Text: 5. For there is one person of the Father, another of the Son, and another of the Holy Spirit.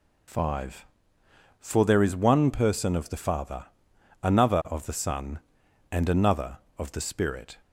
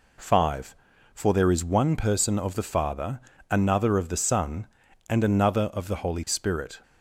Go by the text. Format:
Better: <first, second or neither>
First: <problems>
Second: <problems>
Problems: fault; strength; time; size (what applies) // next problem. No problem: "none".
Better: second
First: skips "Holy"; at 7.0 s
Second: none